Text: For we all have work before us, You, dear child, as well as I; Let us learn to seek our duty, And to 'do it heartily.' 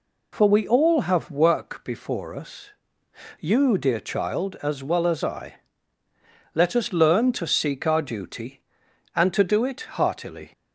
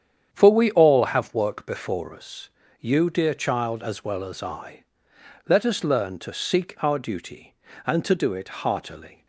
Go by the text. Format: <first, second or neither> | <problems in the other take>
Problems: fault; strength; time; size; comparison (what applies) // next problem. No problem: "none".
first | starts louder than the rest; strong; until 1.4 s; 8.5 dB